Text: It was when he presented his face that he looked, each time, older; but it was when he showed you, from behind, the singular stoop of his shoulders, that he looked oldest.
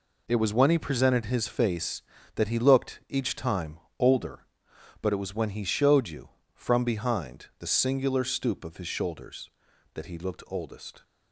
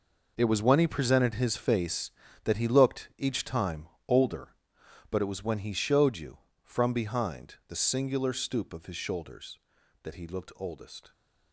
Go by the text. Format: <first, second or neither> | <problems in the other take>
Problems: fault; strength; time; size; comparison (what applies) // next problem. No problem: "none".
first | gets quieter; strong; throughout; 12.5 dB